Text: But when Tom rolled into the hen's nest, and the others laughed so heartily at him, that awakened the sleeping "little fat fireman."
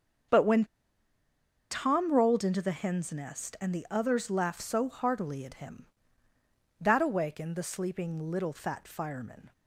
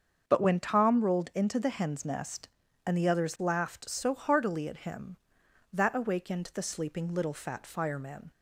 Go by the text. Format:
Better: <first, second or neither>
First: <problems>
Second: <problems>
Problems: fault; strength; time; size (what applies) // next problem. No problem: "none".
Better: second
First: starts louder than the rest; strong; until 2.3 s; 7.5 dB // pauses between "when" and "Tom"; at 0.6 s; 1.0 s long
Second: starts louder than the rest; until 1.2 s; 6.5 dB